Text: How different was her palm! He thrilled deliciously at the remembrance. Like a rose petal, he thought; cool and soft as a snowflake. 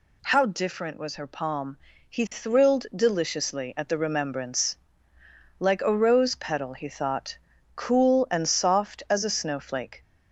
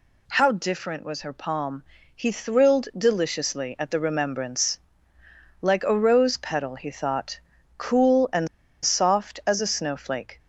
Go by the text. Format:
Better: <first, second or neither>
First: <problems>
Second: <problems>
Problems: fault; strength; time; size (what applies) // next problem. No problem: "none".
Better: first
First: none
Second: pauses between "and" and "soft"; at 8.4 s; 0.36 s long